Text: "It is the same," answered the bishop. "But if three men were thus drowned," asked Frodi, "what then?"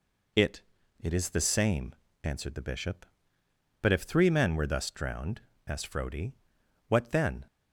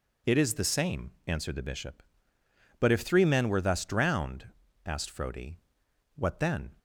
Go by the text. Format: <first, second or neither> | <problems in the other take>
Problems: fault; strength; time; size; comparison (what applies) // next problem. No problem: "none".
second | says "It" twice; at 1.0 s